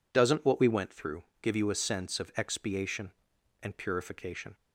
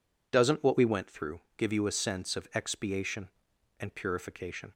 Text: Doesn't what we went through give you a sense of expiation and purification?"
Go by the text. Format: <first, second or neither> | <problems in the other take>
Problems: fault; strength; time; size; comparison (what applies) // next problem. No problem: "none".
neither | pauses between "through" and "give"; slight; the same in both